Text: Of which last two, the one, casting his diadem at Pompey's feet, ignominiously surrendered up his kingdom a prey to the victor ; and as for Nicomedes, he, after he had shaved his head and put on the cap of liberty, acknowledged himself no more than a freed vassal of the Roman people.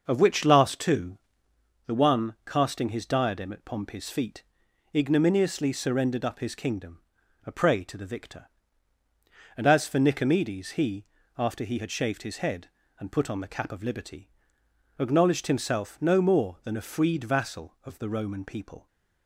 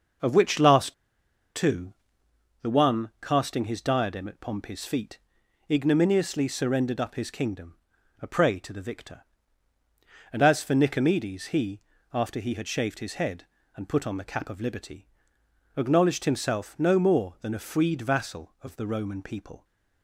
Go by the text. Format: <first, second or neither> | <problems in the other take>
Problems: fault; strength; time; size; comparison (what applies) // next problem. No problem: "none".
first | starts louder than the rest; until 1.8 s; 6 dB; also in the first // pauses between "last" and "two"; noticeable; at 0.9 s; 0.62 s long // pauses between "kingdom" and "a"; at 7.7 s; 0.44 s long; also in the first